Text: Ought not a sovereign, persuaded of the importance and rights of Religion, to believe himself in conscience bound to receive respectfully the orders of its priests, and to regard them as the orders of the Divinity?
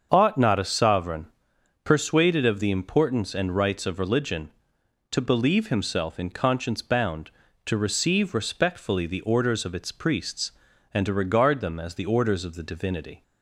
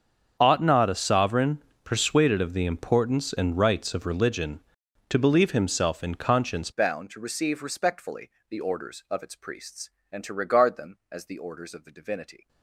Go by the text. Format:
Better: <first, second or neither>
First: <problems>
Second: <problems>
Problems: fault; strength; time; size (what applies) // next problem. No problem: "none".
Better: first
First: starts louder than the rest; until 1.1 s; 7 dB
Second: starts louder than the rest; strong; until 1.4 s; 7 dB // changes voice at "bound"; from 6.7 s on; 5.7 s long // pauses between "respectfully" and "the"; slight; at 8.2 s; 0.20 s long